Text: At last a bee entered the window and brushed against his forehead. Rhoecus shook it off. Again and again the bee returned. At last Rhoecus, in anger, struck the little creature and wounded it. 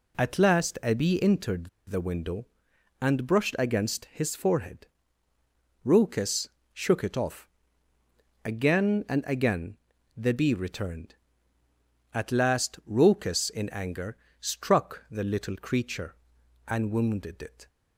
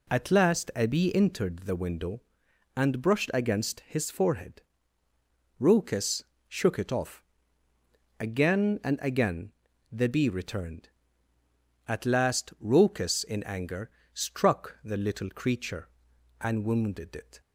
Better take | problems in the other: second | pauses between "entered" and "the"; slight; at 1.6 s; 0.19 s long // pauses between "Rhoecus" and "shook"; slight; at 6.4 s; 0.24 s long; slight in the second // pauses between "again" and "the"; at 9.7 s; 0.40 s long; also in the second

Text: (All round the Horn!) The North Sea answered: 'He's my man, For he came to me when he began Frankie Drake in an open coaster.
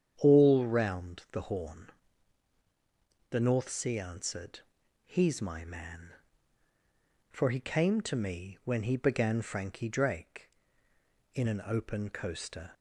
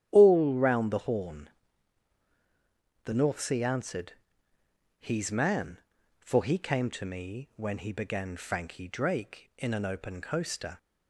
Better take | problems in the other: first | starts louder than the rest; strong; until 1.1 s; 10.5 dB; strong in the first // skips "my"; at 5.3 s

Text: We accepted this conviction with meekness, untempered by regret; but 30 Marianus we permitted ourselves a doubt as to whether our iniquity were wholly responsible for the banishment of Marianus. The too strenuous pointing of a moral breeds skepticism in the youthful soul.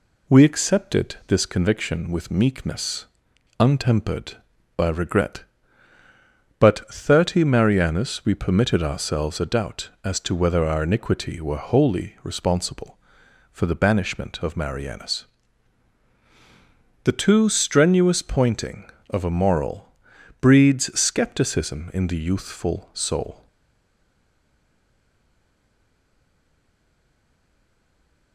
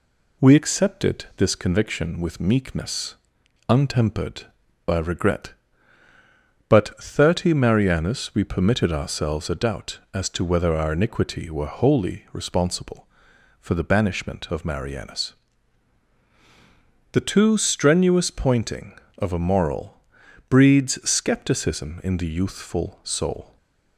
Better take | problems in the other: second | pauses between "moral" and "breeds"; noticeable; at 19.9 s; 0.48 s long; noticeable in the second // stays silent after the last word; strong; from 23.4 s on; 4.9 s long

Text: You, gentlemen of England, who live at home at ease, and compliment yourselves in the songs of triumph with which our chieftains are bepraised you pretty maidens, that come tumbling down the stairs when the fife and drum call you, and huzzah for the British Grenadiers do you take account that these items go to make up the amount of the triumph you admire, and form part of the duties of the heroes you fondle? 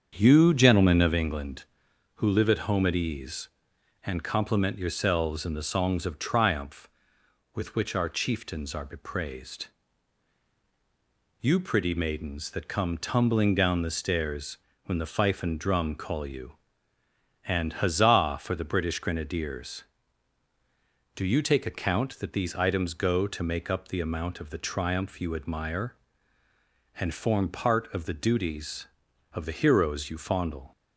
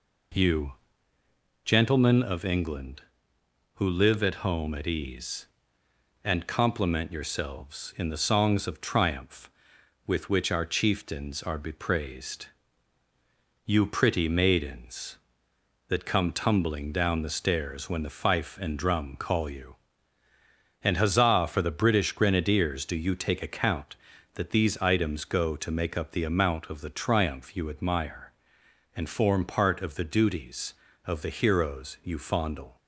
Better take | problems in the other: second | starts louder than the rest; strong; until 1.2 s; 7.5 dB // pauses between "bepraised" and "you"; strong; at 9.6 s; 1.7 s long; also in the second // pauses between "stairs" and "when"; slight; at 14.5 s; 0.30 s long

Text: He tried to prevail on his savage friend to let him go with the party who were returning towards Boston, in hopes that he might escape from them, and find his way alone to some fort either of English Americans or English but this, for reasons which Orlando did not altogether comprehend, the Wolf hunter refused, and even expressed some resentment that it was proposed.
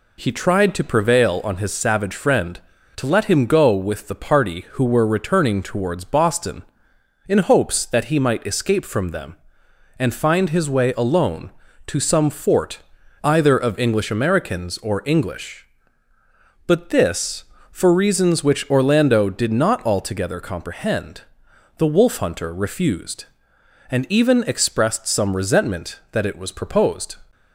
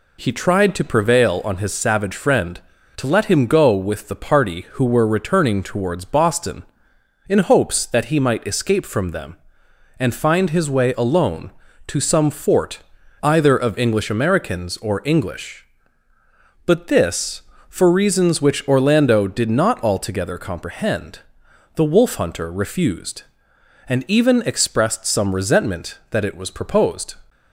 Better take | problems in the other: neither | pauses between "fort" and "either"; the same in both

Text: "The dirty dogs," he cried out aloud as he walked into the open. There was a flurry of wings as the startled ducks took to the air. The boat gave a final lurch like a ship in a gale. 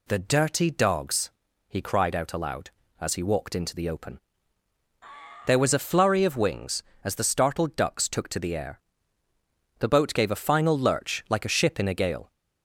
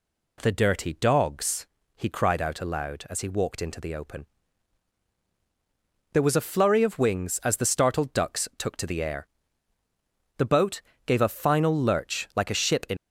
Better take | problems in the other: first | pauses between "boat" and "gave"; slight; at 10.8 s; 0.24 s long // stops before "a gale"; at 12.9 s

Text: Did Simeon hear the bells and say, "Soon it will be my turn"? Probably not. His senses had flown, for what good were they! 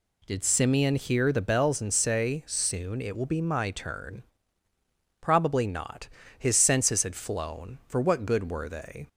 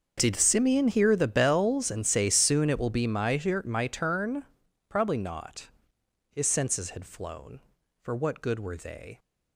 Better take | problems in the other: first | starts louder than the rest; until 1.2 s; 6.5 dB // says "my" twice; at 3.6 s

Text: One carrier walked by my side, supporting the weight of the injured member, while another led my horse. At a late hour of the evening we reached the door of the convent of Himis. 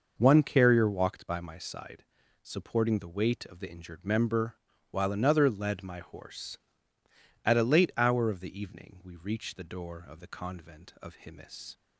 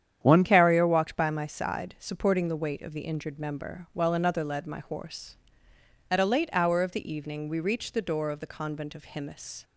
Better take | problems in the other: first | starts louder than the rest; strong; until 1.2 s; 9 dB // changes voice at "carrier"; from 0.4 s on; 9.2 s long

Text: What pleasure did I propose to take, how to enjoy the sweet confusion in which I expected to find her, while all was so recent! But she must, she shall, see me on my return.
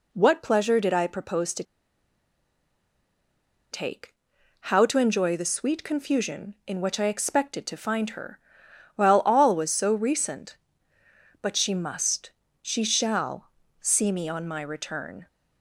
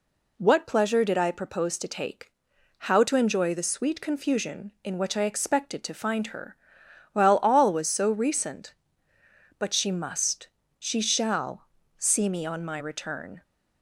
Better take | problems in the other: second | pauses between "to" and "take"; strong; at 1.6 s; 2.0 s long

